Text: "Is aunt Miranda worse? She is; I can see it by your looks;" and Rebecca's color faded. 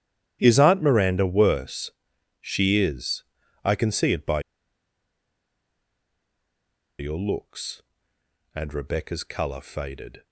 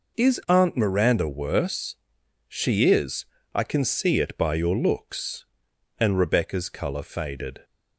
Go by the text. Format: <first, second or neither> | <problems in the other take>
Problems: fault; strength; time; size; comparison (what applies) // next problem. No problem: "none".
second | starts louder than the rest; strong; until 1.4 s; 11 dB // pauses between "by" and "your"; strong; at 4.3 s; 2.5 s long